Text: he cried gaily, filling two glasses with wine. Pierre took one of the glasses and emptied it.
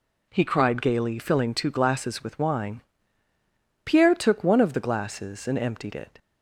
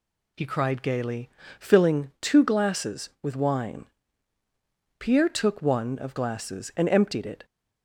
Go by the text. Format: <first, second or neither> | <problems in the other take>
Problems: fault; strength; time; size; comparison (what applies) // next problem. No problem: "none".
first | skips "the"; at 6.1 s